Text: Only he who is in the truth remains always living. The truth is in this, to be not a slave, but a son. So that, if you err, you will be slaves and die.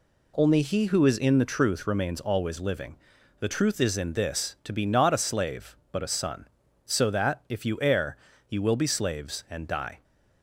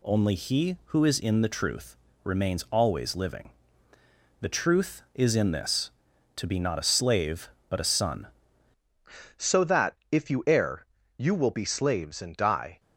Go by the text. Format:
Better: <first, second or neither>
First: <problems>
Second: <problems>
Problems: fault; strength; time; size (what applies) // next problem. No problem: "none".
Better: first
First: none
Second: pauses between "truth" and "remains"; slight; at 1.9 s; 0.28 s long // changes voice at "So"; from 9.3 s on; 3.4 s long